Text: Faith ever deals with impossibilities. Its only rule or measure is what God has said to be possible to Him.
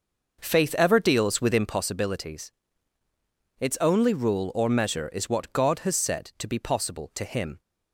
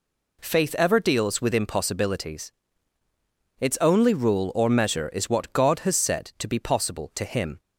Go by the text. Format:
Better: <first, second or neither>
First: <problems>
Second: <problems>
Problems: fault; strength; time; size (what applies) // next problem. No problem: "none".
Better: second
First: starts louder than the rest; noticeable; until 1.8 s; 5.5 dB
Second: none